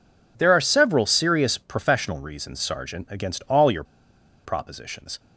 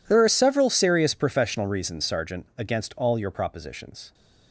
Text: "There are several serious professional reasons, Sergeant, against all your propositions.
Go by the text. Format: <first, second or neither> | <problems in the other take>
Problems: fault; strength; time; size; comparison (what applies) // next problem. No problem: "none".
second | pauses between "your" and "propositions"; noticeable; at 3.8 s; 0.60 s long